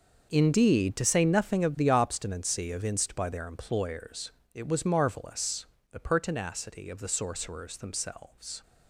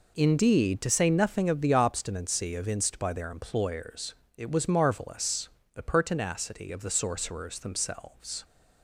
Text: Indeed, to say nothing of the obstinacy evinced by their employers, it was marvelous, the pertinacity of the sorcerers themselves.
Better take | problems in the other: second | gets quieter; strong; throughout; 13 dB

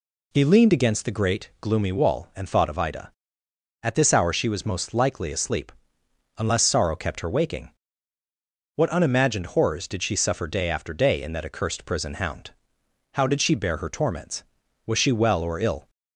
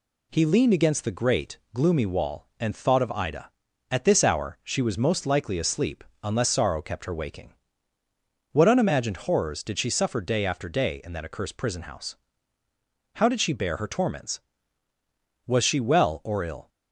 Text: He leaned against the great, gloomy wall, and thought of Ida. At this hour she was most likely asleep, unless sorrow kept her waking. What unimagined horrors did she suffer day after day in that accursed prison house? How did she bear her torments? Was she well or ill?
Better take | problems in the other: second | says "hound" for "house"; at 12.1 s

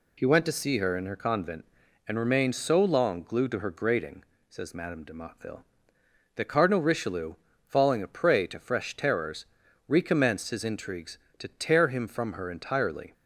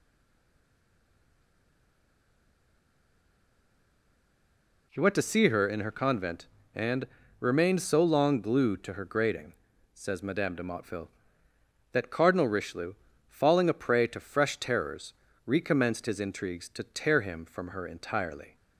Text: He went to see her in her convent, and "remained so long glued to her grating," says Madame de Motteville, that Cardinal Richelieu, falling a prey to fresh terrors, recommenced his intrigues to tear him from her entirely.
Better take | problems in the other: first | stays silent before the first word; strong; until 4.8 s; 4.8 s long // pauses between "and" and "remained"; slight; at 7.0 s; 0.34 s long

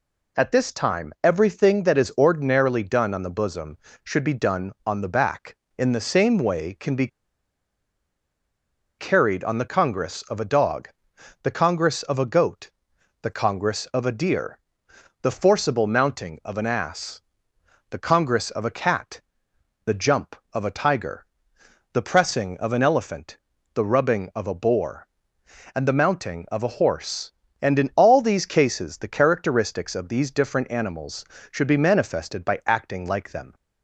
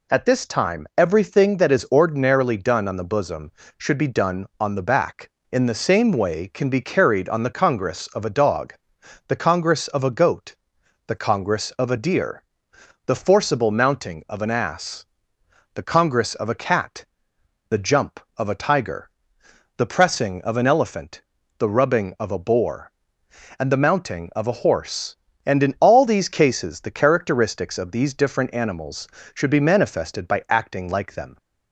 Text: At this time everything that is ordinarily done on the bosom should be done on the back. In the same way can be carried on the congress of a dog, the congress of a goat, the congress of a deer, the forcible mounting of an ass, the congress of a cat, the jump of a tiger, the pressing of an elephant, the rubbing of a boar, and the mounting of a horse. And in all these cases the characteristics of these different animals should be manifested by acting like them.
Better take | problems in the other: second | pauses between "be" and "carried"; strong; at 7.0 s; 1.9 s long

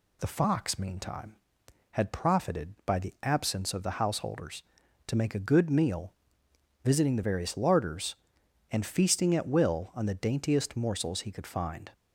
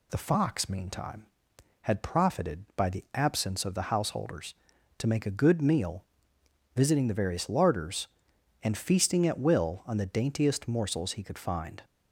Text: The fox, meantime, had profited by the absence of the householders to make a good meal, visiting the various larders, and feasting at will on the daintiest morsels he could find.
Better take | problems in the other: neither | none

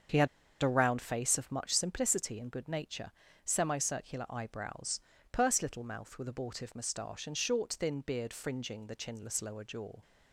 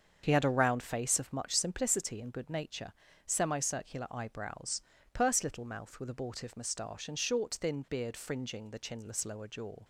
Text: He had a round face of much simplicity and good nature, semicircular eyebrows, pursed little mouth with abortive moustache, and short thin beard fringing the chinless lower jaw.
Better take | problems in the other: second | starts louder than the rest; until 1.4 s; 7 dB; also in the second // pauses between "had" and "a"; slight; at 0.2 s; 0.35 s long

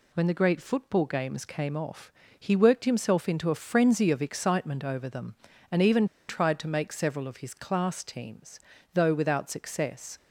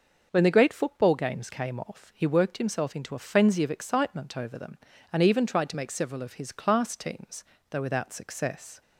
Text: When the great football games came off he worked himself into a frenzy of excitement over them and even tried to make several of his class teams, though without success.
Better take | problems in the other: second | pauses between "off" and "he"; slight; at 2.1 s; 0.26 s long // pauses between "even" and "tried"; slight; at 6.0 s; 0.22 s long

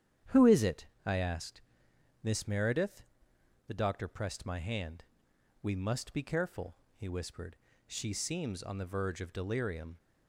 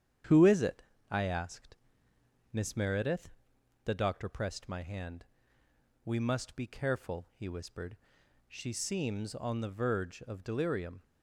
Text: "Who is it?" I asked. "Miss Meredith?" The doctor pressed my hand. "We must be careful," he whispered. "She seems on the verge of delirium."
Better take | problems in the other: neither | starts louder than the rest; strong; the same in both

